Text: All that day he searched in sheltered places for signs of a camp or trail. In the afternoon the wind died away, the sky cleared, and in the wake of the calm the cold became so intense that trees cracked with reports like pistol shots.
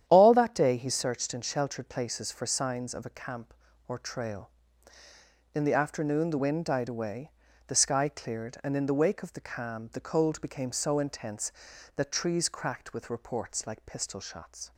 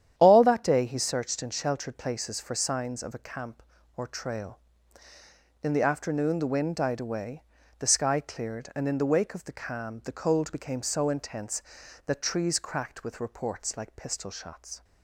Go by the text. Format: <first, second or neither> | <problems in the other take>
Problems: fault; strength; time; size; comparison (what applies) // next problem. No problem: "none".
neither | starts louder than the rest; strong; the same in both